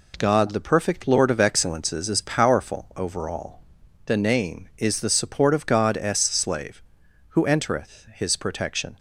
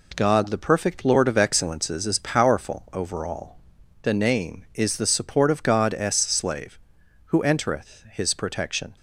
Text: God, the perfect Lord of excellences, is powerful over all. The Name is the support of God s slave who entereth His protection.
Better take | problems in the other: neither | none

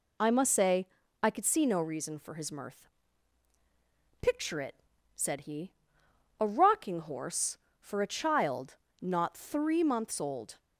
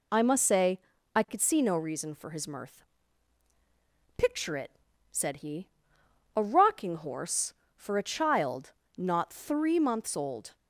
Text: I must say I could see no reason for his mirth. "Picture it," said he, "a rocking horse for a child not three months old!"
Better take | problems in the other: neither | pauses between "say" and "I"; slight; the same in both // pauses between "child" and "not"; slight; the same in both

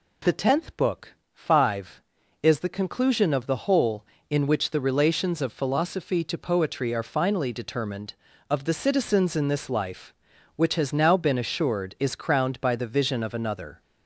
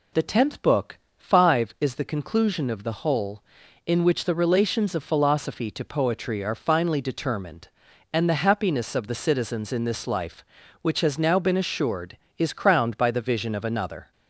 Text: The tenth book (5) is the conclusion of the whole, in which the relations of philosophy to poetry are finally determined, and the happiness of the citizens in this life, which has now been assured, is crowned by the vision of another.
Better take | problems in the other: second | skips "and the happiness"; at 8.3 s

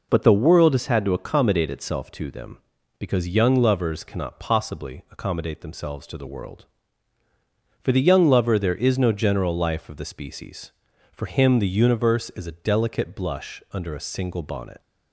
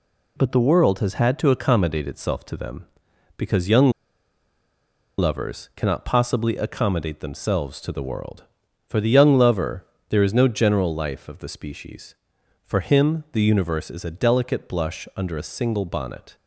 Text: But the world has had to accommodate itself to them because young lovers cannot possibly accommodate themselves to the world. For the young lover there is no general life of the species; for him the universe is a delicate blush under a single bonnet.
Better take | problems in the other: first | pauses between "young" and "lovers"; strong; at 3.9 s; 1.2 s long // pauses between "lover" and "there"; slight; at 9.8 s; 0.24 s long

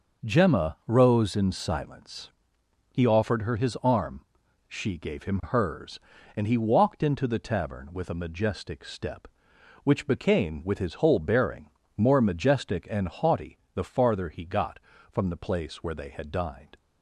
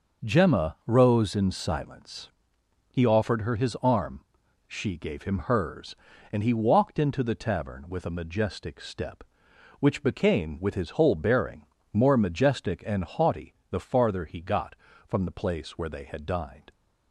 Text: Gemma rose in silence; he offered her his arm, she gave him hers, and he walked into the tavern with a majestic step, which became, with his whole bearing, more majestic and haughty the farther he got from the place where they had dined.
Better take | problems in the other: neither | pauses between "haughty" and "the"; slight; the same in both

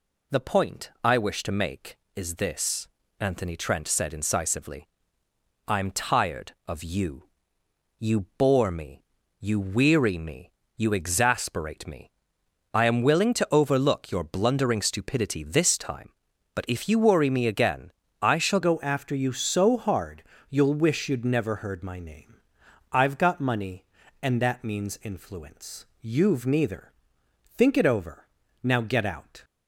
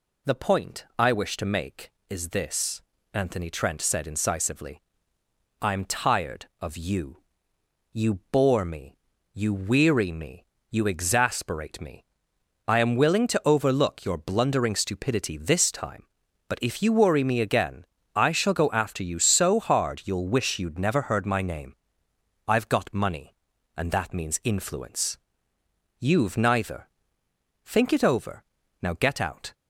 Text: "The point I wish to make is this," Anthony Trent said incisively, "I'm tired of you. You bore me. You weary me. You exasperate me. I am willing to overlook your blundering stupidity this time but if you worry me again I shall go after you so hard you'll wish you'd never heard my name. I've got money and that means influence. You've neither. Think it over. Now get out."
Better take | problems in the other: second | pauses between "You" and "bore"; slight; at 8.2 s; 0.16 s long; slight in the second // pauses between "again" and "I"; slight; at 17.9 s; 0.30 s long; slight in the second // changes voice at "go"; from 18.6 s on; 10.8 s long // pauses between "hard" and "you'll"; slight; at 20.2 s; 0.28 s long

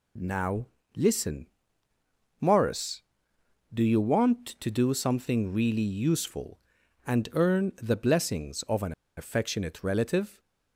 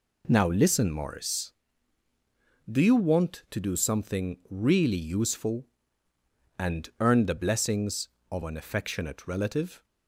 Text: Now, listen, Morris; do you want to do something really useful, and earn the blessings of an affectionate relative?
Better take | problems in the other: second | pauses between "an" and "affectionate"; slight; at 8.9 s; 0.24 s long

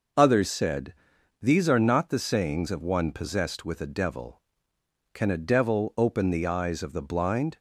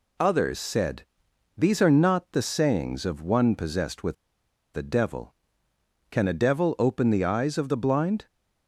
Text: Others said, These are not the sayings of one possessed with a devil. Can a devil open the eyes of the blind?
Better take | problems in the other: first | pauses between "with" and "a"; noticeable; at 4.1 s; 0.61 s long

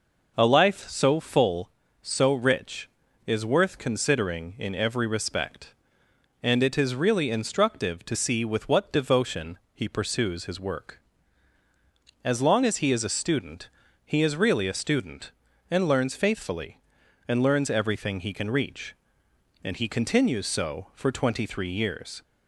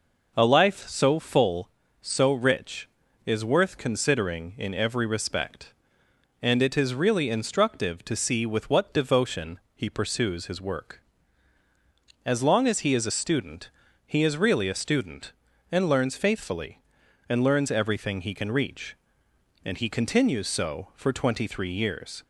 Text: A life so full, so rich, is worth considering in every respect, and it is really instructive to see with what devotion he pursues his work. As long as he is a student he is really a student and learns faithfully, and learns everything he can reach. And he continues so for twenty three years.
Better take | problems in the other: neither | pauses between "devotion" and "he"; slight; the same in both // pauses between "student" and "he"; slight; the same in both

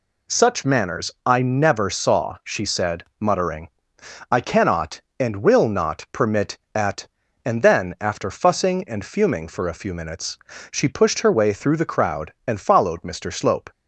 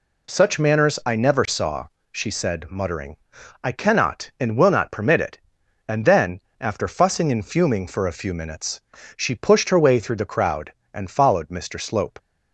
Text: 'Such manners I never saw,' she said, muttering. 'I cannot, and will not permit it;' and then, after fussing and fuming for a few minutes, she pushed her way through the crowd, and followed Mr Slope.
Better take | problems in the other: second | says "at" for "it"; at 6.7 s

